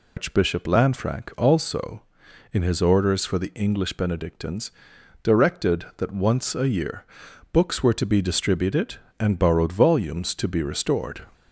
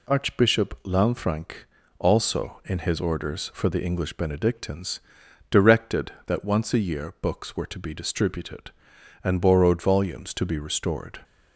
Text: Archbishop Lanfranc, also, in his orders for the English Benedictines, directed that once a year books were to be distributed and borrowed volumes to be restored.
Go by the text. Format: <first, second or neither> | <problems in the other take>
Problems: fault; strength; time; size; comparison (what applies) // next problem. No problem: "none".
second | loses the start of "Archbishop"; at 0.1 s; 145 ms // pauses between "year" and "books"; noticeable; at 7.0 s; 0.48 s long